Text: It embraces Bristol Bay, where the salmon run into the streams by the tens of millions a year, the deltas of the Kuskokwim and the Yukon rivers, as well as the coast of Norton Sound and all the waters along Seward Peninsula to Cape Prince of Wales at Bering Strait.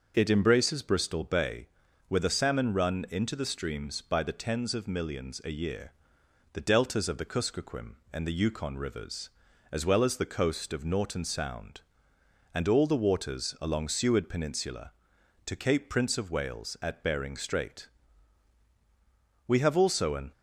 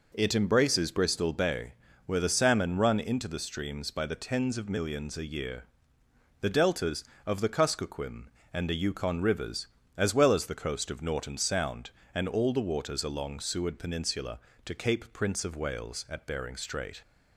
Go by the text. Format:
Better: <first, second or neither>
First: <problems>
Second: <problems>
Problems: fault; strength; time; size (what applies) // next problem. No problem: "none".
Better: second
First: starts louder than the rest; until 1.1 s; 6.5 dB // goes on to say "We have also an"; noticeable; from 19.4 s on; 0.84 s long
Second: none